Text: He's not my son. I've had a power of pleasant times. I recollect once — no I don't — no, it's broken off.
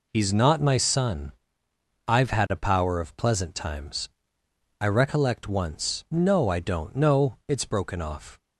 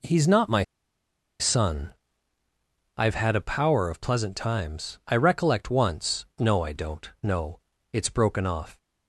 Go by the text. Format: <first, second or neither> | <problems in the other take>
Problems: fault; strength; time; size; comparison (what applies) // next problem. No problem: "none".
first | pauses between "my" and "son"; noticeable; at 0.6 s; 0.77 s long